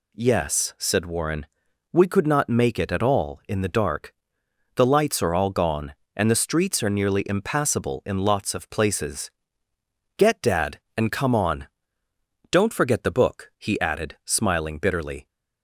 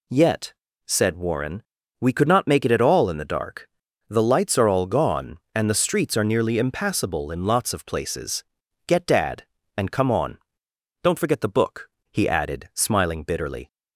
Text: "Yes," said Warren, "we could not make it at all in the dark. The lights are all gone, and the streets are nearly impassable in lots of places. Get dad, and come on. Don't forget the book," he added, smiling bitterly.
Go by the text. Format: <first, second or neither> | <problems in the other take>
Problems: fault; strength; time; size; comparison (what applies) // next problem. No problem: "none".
first | says "Yet" for "Yes"; at 0.0 s